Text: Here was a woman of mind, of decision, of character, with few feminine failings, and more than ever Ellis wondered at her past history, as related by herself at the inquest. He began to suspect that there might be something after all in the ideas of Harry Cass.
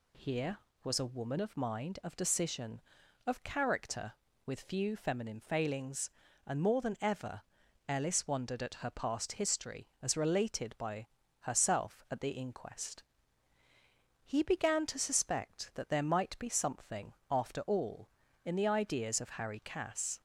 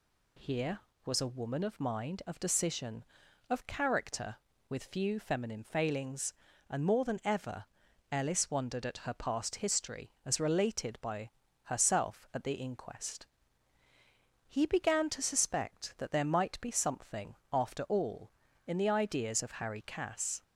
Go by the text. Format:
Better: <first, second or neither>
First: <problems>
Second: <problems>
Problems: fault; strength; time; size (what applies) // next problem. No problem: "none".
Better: neither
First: pauses between "ever" and "Ellis"; noticeable; at 7.4 s; 0.46 s long // pauses between "by" and "herself"; slight; at 11.0 s; 0.32 s long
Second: pauses between "ever" and "Ellis"; noticeable; at 7.6 s; 0.46 s long // pauses between "by" and "herself"; slight; at 11.3 s; 0.32 s long